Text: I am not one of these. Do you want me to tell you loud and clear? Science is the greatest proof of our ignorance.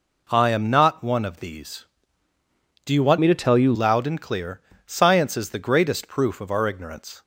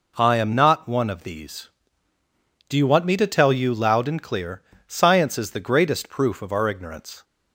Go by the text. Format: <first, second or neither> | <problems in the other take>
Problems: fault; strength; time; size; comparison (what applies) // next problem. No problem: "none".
second | changes voice from "me" to "you"; from 3.2 to 3.7 s; 0.5 s long